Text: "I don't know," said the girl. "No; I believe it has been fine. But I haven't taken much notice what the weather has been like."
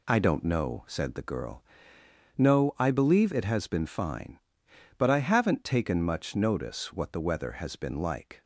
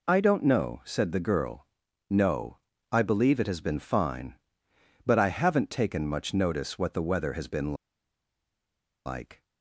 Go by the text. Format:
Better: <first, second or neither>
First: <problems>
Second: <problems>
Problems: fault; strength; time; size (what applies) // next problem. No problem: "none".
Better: first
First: none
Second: pauses between "been" and "like"; strong; at 7.7 s; 1.3 s long